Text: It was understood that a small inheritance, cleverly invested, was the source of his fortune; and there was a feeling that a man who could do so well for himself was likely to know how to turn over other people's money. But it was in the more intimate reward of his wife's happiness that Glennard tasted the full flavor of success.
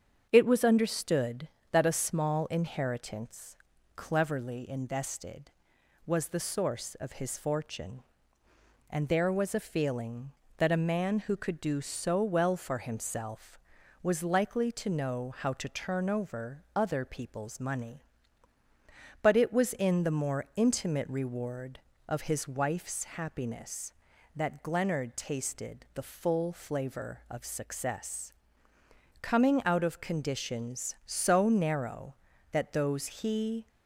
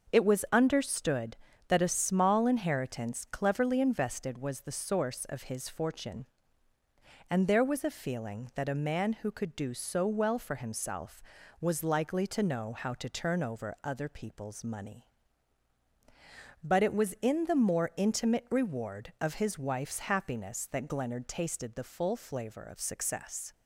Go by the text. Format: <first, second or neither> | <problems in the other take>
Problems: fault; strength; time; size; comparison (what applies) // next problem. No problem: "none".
second | starts louder than the rest; until 1.3 s; 7 dB; also in the second // goes on to say "Coming out of conditions so narrow that those he"; strong; from 29.1 s on; 4.4 s long